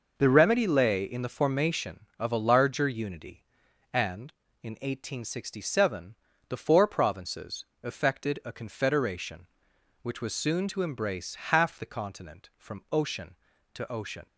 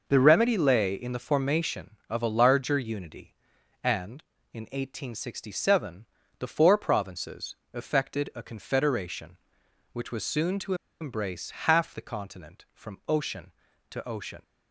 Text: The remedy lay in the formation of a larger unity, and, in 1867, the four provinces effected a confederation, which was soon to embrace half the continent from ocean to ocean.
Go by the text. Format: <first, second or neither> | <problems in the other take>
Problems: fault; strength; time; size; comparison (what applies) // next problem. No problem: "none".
first | pauses between "provinces" and "effected"; slight; at 7.5 s; 0.18 s long; slight in the first // pauses between "to" and "embrace"; slight; at 10.7 s; 0.26 s long